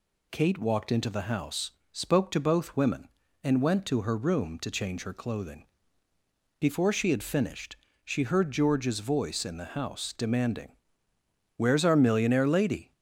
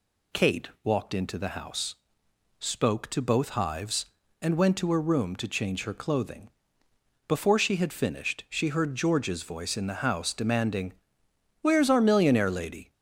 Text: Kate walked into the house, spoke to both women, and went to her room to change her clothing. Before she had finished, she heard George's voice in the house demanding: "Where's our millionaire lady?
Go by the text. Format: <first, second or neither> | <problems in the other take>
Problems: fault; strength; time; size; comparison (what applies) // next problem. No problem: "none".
first | says "hives" for "women"; at 3.4 s